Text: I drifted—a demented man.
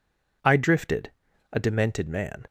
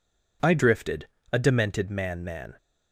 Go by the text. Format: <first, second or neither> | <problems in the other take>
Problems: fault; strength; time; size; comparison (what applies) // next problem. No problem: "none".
first | says "man" twice; at 2.2 s